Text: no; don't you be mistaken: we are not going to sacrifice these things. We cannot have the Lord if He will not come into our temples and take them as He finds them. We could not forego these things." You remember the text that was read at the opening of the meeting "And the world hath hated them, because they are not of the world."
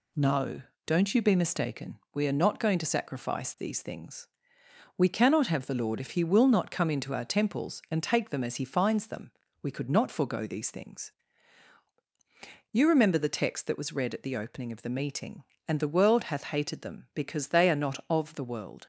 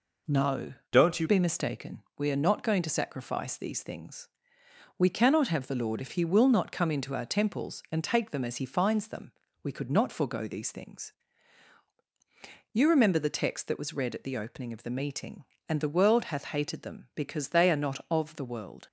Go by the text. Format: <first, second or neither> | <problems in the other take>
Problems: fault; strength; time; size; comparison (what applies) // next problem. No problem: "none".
first | changes voice from "don't" to "you"; from 0.9 to 1.2 s; 0.3 s long